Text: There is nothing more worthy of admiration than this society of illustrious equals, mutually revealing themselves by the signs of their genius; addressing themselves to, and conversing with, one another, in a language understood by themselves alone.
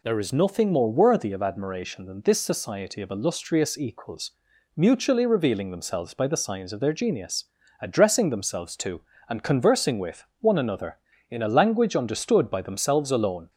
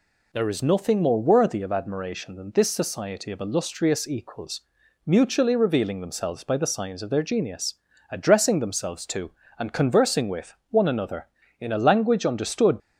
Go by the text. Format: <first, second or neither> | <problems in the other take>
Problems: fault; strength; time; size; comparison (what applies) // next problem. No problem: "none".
first | stops before "by themselves alone"; at 12.7 s